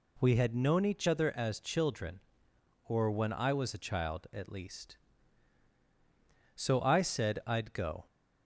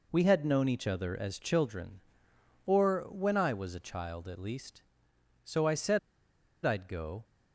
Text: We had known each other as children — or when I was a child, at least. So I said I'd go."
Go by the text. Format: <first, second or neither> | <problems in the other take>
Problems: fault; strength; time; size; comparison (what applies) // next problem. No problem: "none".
first | pauses between "said" and "I'd"; noticeable; at 5.9 s; 0.66 s long